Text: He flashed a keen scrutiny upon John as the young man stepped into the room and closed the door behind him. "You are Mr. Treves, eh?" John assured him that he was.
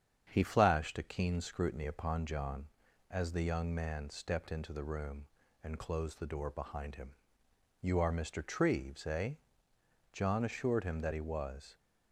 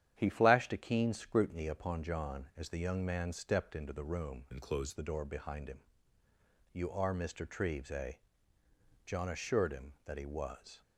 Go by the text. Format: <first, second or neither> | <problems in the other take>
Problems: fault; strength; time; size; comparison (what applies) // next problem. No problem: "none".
first | starts louder than the rest; strong; until 1.1 s; 10 dB; strong in the first // changes voice from "and" to "closed"; from 4.5 to 4.9 s; 0.4 s long